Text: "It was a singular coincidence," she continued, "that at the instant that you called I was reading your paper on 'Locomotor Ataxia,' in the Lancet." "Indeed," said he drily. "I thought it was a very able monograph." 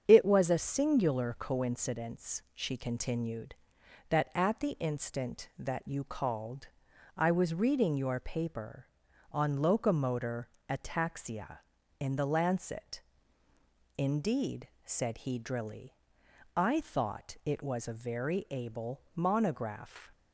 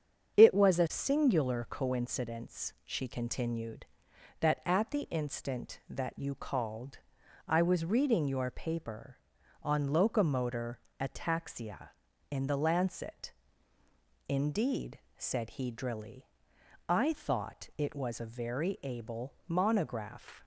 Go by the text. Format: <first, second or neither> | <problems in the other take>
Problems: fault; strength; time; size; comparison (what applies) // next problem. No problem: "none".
neither | starts louder than the rest; strong; the same in both // pauses between "called" and "I"; noticeable; the same in both // pauses between "Locomotor" and "Ataxia"; slight; the same in both